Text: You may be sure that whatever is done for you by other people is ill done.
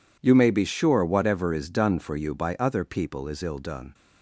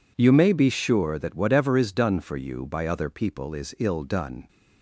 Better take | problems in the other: second | skips "that"; at 1.0 s

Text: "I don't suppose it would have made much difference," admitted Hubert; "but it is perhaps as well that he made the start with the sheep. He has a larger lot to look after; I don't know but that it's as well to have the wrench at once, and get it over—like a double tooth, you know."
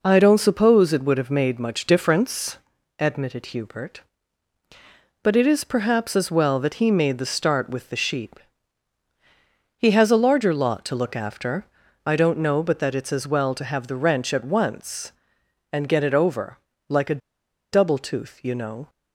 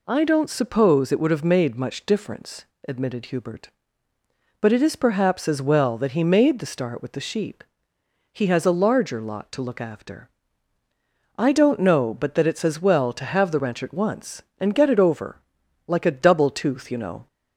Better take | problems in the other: second | pauses between "a" and "double"; noticeable; at 17.2 s; 0.52 s long

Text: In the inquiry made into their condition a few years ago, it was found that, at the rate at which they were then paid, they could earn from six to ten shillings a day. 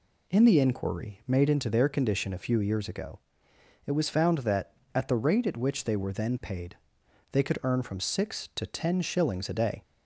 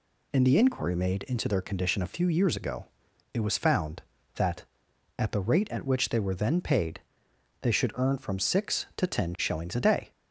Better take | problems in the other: first | says "should" for "could"; at 7.7 s

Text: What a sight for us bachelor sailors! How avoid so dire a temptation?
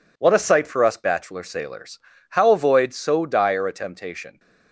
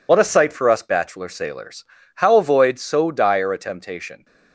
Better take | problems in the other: first | loses the start of "What"; at 0.0 s; 65 ms

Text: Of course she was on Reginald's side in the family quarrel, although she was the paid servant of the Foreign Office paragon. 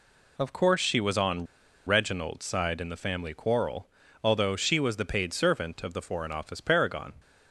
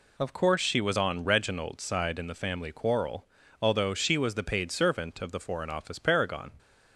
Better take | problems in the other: second | pauses between "on" and "Reginald's"; at 1.4 s; 0.41 s long

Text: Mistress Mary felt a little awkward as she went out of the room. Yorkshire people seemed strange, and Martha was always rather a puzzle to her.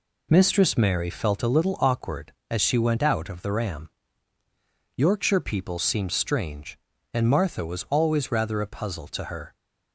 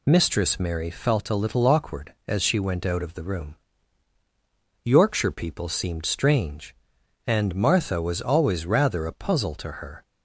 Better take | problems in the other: second | says "ram" for "room"; at 3.5 s

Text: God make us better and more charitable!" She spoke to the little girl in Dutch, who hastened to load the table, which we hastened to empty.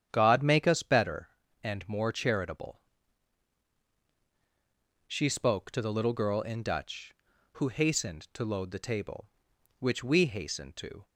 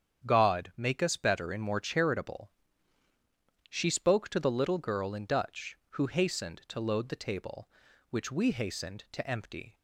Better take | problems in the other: second | starts louder than the rest; strong; until 1.1 s; 9 dB; strong in the second // stops before "empty"; at 11.0 s

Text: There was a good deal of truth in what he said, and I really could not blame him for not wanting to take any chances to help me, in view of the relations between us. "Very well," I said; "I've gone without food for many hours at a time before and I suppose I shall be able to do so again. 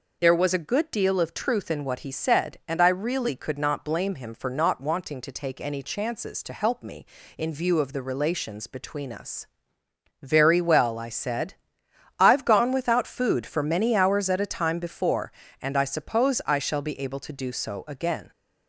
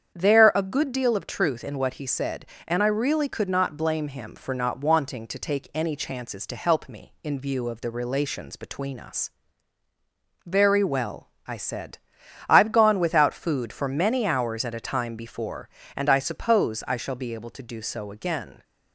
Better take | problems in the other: first | starts louder than the rest; strong; until 1.1 s; 8 dB // skips "was"; at 0.5 s

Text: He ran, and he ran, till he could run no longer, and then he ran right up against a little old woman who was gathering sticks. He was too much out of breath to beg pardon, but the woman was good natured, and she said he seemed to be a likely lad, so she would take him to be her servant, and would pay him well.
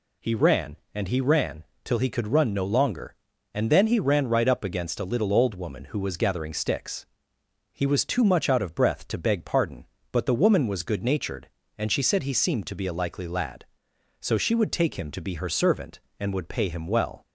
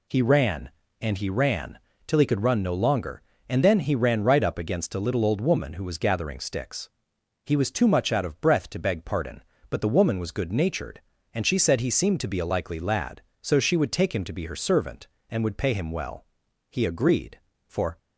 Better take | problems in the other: first | goes on to say "He agreed for"; noticeable; from 16.6 s on; 1.2 s long

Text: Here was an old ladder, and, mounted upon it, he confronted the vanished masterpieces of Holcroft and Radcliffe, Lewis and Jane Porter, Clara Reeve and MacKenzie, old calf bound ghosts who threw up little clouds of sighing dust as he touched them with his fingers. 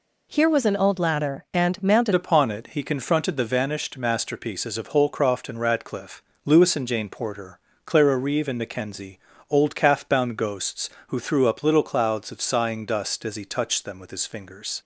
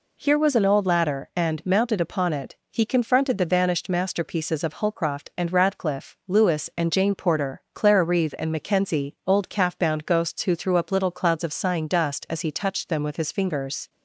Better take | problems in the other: second | changes voice at "upon"; from 2.1 s on; 12.7 s long

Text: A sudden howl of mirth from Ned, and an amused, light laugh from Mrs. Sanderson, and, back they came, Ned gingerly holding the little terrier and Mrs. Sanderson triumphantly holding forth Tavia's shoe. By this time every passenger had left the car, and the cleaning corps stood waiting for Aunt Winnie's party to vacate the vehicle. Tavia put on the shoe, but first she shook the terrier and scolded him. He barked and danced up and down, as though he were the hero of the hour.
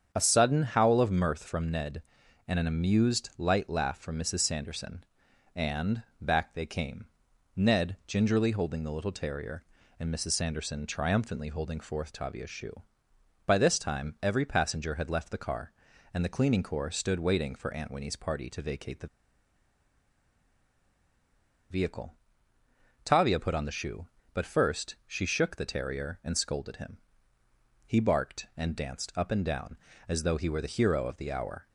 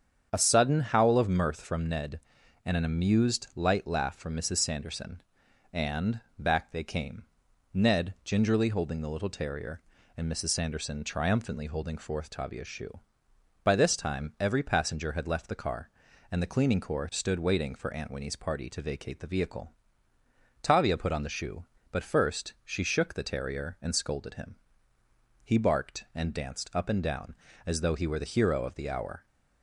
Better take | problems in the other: second | starts louder than the rest; strong; until 1.1 s; 8 dB; strong in the second // pauses between "the" and "vehicle"; strong; at 19.0 s; 2.6 s long

